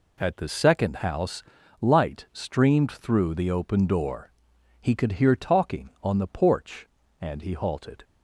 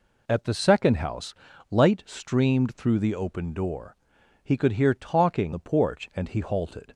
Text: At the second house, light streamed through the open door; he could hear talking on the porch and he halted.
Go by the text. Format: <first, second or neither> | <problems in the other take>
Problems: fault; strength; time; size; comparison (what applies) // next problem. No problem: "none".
first | skips "on"; at 5.5 s